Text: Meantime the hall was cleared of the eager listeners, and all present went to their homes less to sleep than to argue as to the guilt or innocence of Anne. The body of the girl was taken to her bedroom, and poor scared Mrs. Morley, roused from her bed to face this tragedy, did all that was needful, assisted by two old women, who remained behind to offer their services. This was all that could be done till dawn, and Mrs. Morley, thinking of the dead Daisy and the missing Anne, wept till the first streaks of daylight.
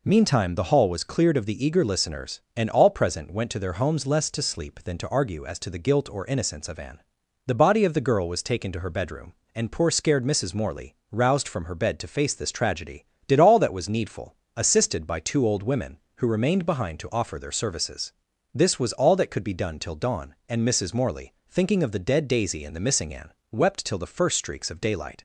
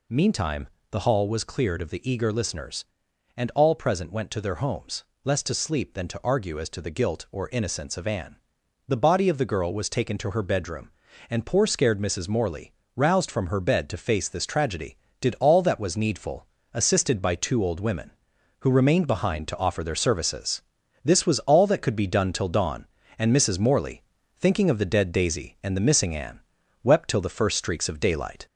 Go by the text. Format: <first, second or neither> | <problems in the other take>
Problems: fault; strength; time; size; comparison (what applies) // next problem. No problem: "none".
first | gets louder; slight; throughout; 2.5 dB // pauses between "Meantime" and "the"; slight; at 0.6 s; 0.24 s long // pauses between "homes" and "less"; slight; at 5.0 s; 0.20 s long